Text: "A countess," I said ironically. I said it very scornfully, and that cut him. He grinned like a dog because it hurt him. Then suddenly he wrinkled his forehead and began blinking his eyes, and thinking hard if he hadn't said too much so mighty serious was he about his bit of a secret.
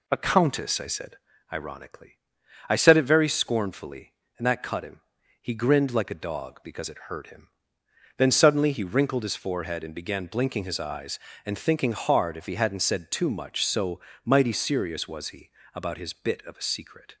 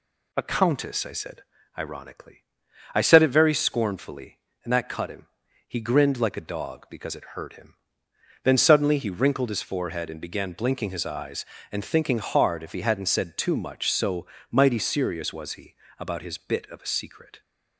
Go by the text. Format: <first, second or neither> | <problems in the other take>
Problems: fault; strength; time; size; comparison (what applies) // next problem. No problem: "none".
second | starts louder than the rest; slight; until 1.1 s; 2.5 dB // pauses between "said" and "ironically"; slight; at 1.1 s; 0.34 s long; slight in the second // pauses between "so" and "mighty"; slight; at 13.9 s; 0.24 s long; slight in the second // pauses between "he" and "about"; slight; at 15.4 s; 0.24 s long; slight in the second